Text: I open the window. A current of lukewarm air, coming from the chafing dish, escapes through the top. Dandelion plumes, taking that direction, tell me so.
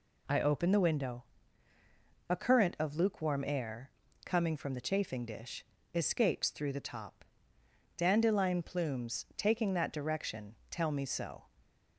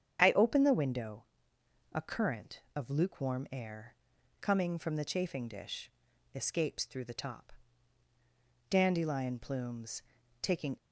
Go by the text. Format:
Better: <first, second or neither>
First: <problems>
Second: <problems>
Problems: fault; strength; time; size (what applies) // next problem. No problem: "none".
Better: first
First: none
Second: starts louder than the rest; strong; until 1.2 s; 8 dB // stops before "that direction tell me so"; at 10.7 s